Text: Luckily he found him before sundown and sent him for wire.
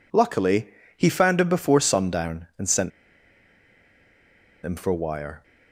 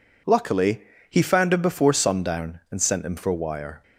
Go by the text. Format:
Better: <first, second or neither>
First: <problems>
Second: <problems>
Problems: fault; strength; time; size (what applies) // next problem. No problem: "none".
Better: second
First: pauses between "Luckily" and "he"; slight; at 0.6 s; 0.28 s long // pauses between "sent" and "him"; strong; at 2.9 s; 1.7 s long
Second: pauses between "Luckily" and "he"; slight; at 0.8 s; 0.27 s long